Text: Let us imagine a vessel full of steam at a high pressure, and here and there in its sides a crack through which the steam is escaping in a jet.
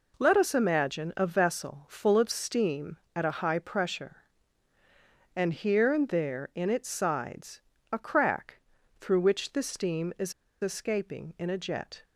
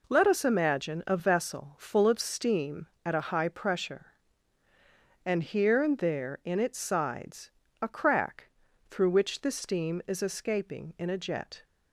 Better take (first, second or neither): second